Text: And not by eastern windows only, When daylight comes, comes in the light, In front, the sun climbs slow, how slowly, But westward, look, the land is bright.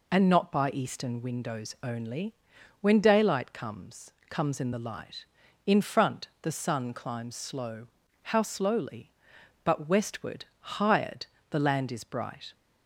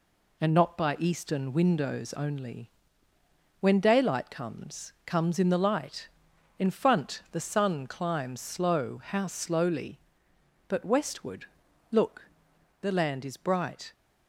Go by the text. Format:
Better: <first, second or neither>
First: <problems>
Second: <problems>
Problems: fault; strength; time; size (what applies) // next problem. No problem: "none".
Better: second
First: says "hired" for "look"; at 10.5 s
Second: none